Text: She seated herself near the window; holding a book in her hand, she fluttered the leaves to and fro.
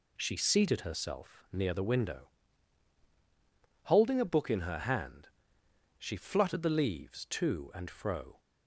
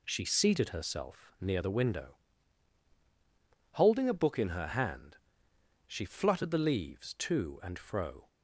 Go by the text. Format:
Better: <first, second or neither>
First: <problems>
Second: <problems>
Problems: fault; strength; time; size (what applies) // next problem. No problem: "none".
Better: neither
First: none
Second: none